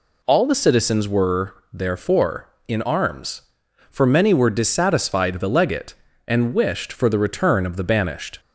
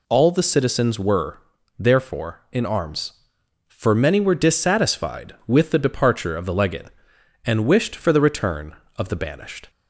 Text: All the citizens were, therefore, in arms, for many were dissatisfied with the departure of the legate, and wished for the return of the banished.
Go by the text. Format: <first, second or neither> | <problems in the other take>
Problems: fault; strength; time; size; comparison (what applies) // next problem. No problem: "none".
second | skips "with the departure of"; at 5.3 s